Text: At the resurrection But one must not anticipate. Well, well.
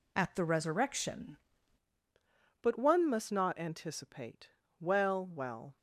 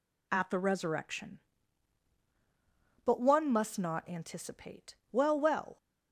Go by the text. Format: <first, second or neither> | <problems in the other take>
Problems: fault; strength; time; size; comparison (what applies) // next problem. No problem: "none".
second | changes voice at "But"; from 2.6 s on; 3.1 s long